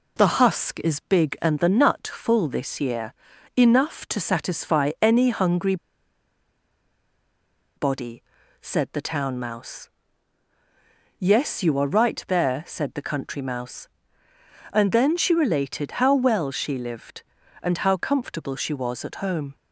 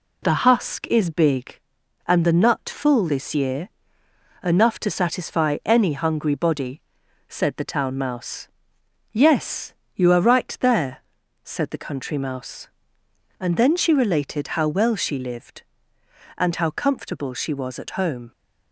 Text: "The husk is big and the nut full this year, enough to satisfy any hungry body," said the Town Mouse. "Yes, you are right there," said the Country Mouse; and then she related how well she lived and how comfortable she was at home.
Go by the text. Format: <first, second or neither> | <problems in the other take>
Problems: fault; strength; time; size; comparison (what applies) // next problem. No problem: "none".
second | pauses between "hungry" and "body"; strong; at 5.7 s; 2.0 s long